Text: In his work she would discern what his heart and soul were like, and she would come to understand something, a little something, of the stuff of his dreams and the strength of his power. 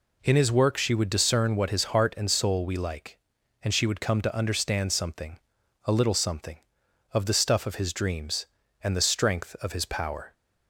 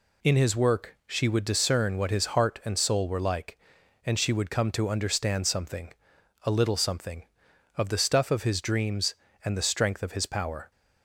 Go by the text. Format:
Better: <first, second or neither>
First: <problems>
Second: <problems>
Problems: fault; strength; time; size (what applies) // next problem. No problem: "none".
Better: second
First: says "we" for "were"; at 2.6 s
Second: none